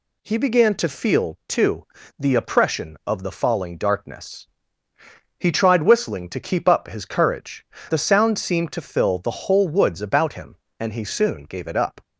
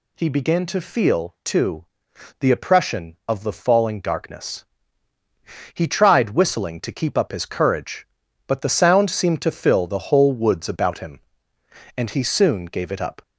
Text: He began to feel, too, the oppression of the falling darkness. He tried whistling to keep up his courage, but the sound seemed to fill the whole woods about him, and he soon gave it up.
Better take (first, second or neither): second